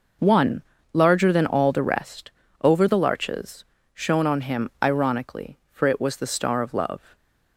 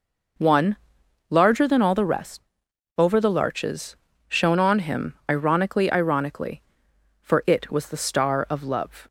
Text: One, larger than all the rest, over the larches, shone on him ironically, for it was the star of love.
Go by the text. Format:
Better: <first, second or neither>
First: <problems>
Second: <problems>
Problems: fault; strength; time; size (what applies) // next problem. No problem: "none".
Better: first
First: none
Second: pauses between "him" and "ironically"; slight; at 5.1 s; 0.16 s long // says "ironically" twice; at 5.9 s